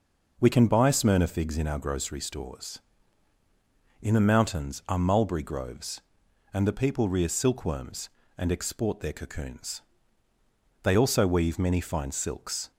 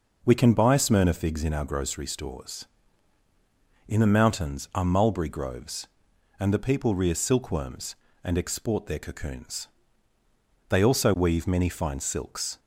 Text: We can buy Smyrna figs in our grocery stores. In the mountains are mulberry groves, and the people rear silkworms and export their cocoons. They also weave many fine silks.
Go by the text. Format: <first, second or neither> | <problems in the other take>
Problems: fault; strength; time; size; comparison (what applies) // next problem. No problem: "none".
neither | none